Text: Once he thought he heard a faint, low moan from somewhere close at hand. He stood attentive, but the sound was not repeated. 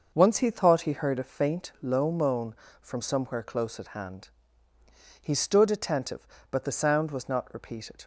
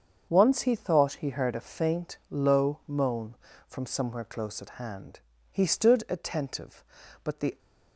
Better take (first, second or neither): first